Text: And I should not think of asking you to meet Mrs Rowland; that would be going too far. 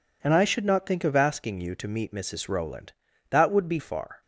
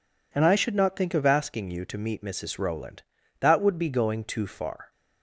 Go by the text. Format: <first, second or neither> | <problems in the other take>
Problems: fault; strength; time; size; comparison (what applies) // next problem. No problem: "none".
second | skips "going too"; at 3.7 s